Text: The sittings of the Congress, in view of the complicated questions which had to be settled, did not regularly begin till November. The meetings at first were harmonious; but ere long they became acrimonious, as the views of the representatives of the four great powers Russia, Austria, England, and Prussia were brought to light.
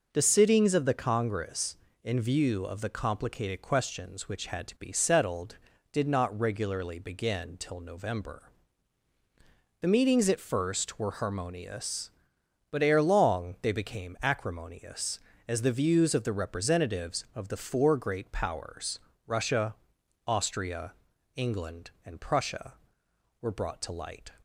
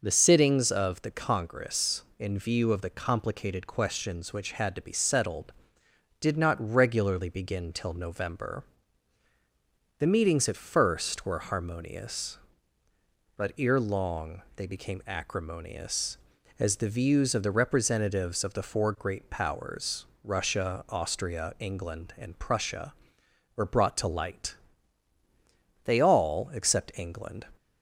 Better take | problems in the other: first | pauses between "powers" and "Russia"; slight; at 20.0 s; 0.18 s long; slight in the first // goes on to say "They all except England"; from 25.8 s on; 1.5 s long

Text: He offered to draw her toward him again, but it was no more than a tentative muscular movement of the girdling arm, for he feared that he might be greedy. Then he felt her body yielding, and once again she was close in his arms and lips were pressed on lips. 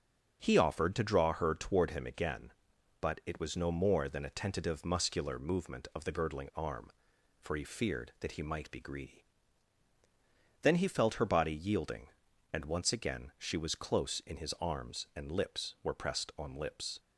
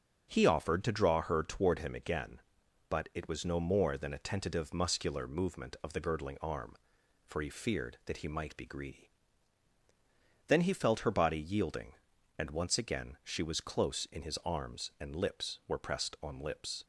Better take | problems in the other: neither | starts louder than the rest; the same in both

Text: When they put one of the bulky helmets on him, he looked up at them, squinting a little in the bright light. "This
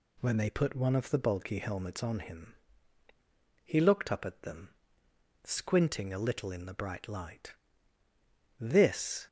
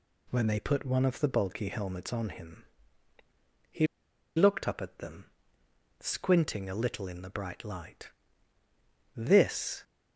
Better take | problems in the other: first | pauses between "he" and "looked"; noticeable; at 3.8 s; 0.49 s long

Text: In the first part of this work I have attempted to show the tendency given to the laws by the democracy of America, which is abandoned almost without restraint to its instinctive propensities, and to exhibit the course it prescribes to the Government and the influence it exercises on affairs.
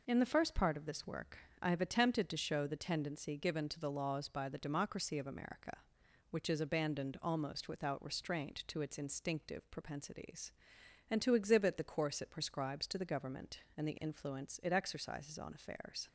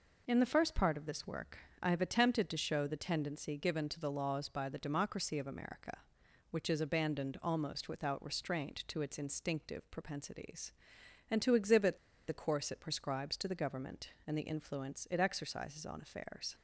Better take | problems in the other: first | pauses between "work" and "I"; slight; at 1.5 s; 0.24 s long; slight in the first // pauses between "exhibit" and "the"; slight; at 11.9 s; 0.30 s long

